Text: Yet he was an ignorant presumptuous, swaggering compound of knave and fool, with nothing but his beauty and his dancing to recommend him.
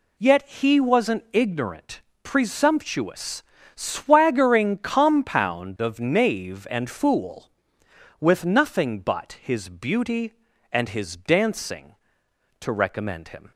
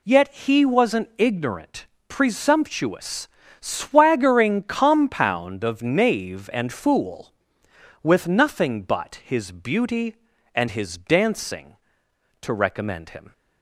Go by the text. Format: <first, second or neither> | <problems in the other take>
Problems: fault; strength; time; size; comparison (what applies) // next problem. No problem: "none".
neither | pauses between "ignorant" and "presumptuous"; slight; the same in both